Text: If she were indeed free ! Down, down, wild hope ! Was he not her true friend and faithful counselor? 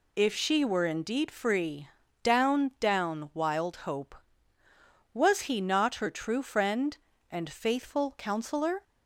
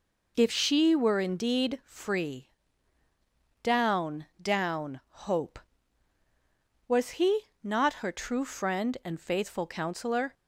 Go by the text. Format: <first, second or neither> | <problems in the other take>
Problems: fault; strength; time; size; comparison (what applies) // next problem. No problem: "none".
first | skips "wild"; at 5.0 s // pauses between "he" and "not"; slight; at 7.4 s; 0.20 s long